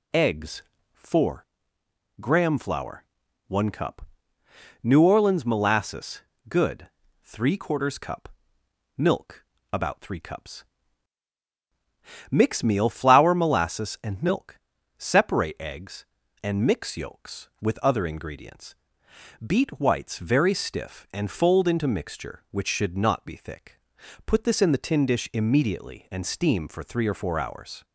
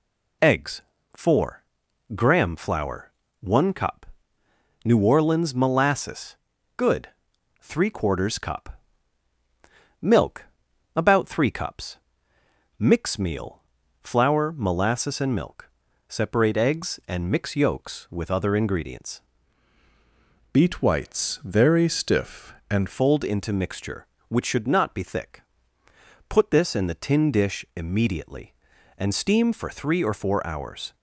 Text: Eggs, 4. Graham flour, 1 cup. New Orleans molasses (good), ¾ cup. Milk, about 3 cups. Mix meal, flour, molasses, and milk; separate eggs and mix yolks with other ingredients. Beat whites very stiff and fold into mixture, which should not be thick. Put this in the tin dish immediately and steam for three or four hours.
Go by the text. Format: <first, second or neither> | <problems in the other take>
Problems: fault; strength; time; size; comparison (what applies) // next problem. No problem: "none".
first | changes voice from "Beat" to "and"; from 20.5 to 22.8 s; 2.3 s long